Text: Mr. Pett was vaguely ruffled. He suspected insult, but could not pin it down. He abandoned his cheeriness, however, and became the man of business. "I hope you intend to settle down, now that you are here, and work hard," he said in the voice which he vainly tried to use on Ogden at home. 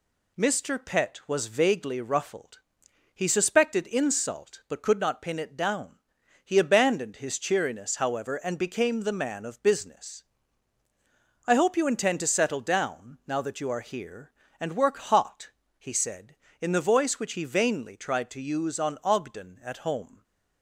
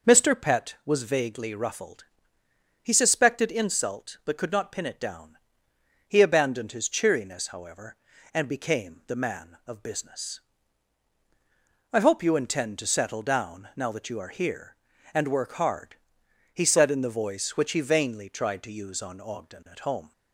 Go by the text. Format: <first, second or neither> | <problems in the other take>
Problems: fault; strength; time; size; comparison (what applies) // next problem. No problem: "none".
second | says "hot" for "hard"; at 14.9 s